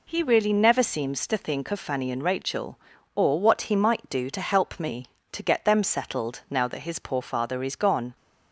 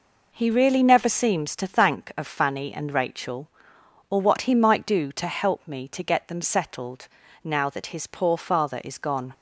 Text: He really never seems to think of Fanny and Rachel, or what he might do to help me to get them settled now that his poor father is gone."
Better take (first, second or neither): first